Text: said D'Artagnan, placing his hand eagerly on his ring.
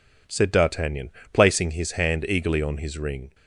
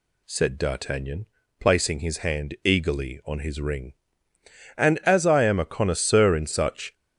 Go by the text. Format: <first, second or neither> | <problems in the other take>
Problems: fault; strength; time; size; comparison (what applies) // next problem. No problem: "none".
first | goes on to say "And as I am a connoisseur in such"; strong; from 4.7 s on; 2.1 s long